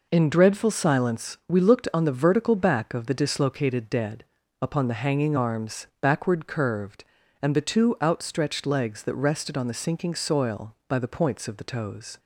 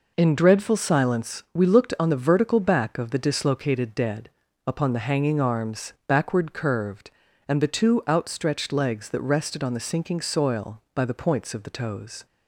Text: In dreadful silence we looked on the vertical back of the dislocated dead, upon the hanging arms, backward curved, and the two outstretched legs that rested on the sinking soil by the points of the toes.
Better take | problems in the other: neither | none

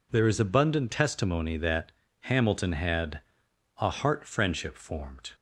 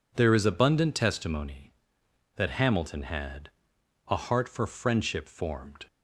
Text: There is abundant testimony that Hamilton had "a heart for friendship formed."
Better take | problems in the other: second | pauses between "that" and "Hamilton"; slight; at 1.9 s; 0.30 s long // pauses between "had" and "a"; noticeable; at 3.2 s; 0.58 s long; noticeable in the second // skips "for"; at 4.2 s

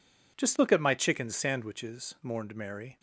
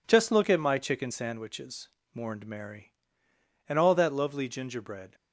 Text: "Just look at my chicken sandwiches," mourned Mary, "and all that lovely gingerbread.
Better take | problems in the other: second | stops before "and all that lovely gingerbread"; at 2.9 s

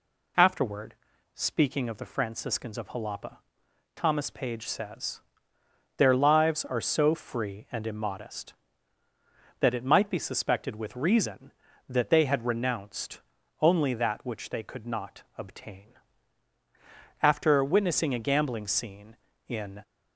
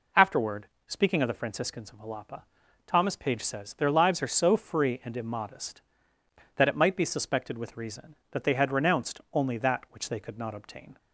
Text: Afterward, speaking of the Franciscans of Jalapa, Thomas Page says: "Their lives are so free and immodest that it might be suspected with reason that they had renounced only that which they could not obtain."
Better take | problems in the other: second | pauses between "renounced" and "only"; at 13.2 s; 0.40 s long // goes on to say "After witnessing a gambling scene in"; strong; from 17.2 s on; 2.6 s long

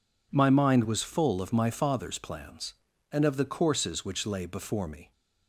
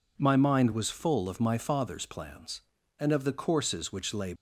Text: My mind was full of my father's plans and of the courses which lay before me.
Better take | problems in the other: first | stops before "before me"; at 4.3 s

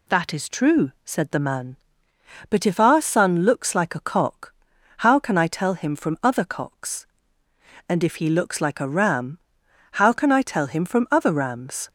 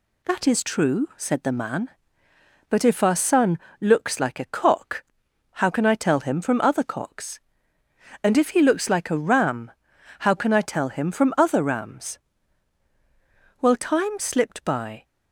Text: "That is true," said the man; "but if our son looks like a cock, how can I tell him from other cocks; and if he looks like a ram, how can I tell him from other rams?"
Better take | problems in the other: first | pauses between "son" and "looks"; slight; at 3.5 s; 0.22 s long // goes on to say "Well time slipped by"; from 13.6 s on; 1.4 s long

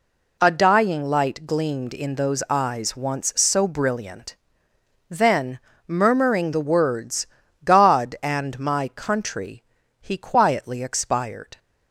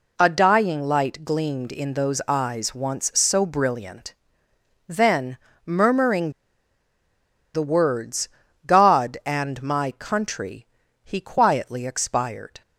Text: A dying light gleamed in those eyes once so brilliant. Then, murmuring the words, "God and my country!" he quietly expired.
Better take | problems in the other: first | pauses between "murmuring" and "the"; at 6.2 s; 1.2 s long

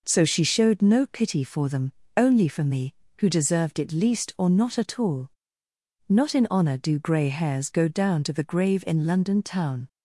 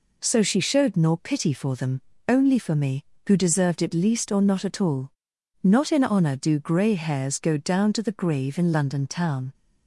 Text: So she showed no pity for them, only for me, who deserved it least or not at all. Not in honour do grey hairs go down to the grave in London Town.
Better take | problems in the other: first | says "nor" for "no"; at 0.9 s

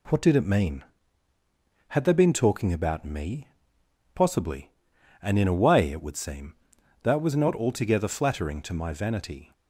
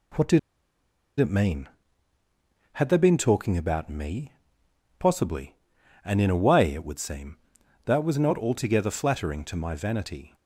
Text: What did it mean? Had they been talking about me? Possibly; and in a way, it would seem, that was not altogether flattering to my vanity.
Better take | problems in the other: first | pauses between "did" and "it"; noticeable; at 0.3 s; 0.81 s long

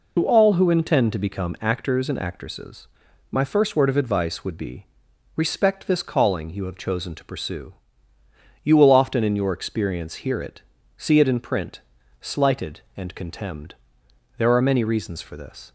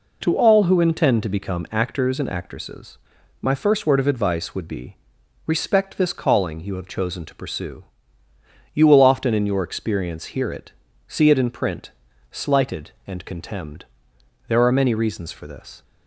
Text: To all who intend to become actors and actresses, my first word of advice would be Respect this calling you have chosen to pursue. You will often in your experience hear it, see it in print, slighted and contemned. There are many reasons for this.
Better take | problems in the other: second | loses the start of "To"; at 0.1 s; 60 ms // pauses between "be" and "Respect"; noticeable; at 4.8 s; 0.52 s long; noticeable in the second

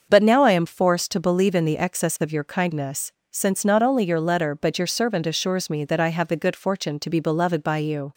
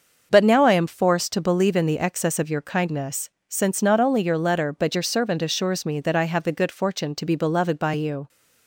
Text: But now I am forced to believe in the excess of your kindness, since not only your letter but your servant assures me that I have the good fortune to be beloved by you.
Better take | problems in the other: neither | starts louder than the rest; the same in both

